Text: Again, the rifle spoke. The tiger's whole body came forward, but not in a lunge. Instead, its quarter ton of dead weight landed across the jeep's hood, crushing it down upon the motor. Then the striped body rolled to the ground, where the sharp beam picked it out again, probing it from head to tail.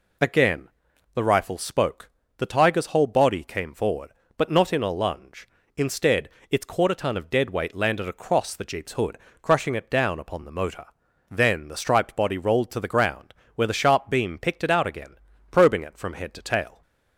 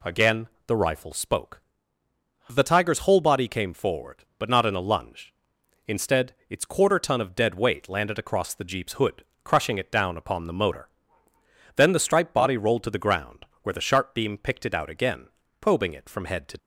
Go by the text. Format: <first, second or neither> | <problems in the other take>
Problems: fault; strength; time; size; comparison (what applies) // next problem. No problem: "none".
first | stops before "tail"; at 16.5 s